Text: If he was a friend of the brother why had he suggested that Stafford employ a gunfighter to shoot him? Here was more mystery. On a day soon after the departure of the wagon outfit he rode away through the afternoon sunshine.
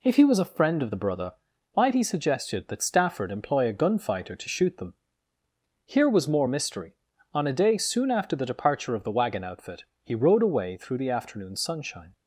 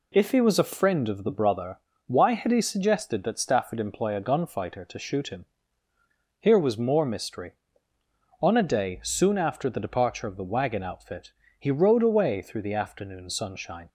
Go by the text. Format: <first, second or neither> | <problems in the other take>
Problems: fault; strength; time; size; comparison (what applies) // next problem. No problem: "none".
second | pauses between "brother" and "why"; at 1.3 s; 0.38 s long; slight in the second // says "them" for "him"; at 4.7 s // pauses between "outfit" and "he"; slight; at 9.8 s; 0.18 s long; slight in the second